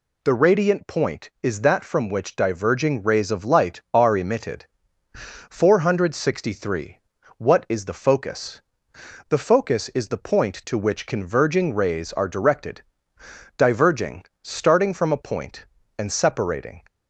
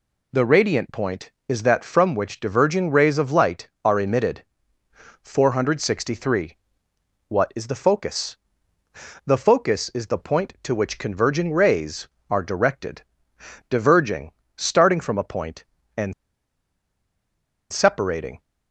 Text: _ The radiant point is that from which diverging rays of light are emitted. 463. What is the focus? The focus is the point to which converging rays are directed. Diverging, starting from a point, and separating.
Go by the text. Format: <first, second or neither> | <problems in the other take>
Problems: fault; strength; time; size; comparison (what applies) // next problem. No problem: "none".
first | pauses between "and" and "separating"; strong; at 16.1 s; 1.5 s long